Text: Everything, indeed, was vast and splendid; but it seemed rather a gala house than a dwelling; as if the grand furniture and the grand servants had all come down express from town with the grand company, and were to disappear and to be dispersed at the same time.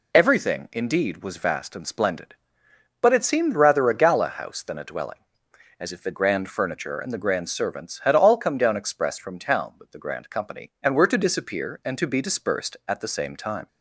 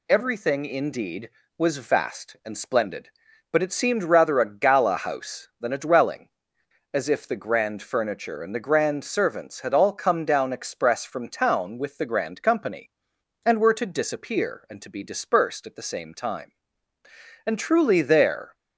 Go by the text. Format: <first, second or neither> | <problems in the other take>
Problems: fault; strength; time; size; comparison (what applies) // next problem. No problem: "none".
first | goes on to say "And truly there"; noticeable; from 17.4 s on; 1.1 s long